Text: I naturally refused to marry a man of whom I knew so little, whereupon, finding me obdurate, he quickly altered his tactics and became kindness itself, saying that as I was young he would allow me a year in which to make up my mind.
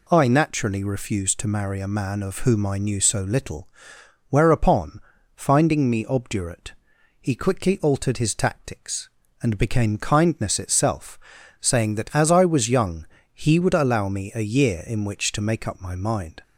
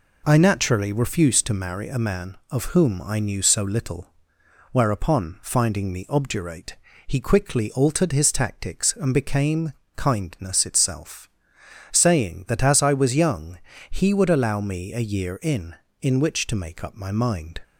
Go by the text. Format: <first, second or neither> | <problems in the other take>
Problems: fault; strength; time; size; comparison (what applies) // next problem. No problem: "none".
first | pauses between "became" and "kindness"; slight; at 9.7 s; 0.22 s long // pauses between "young" and "he"; slight; at 13.5 s; 0.32 s long; slight in the first // says "in" twice; at 15.9 s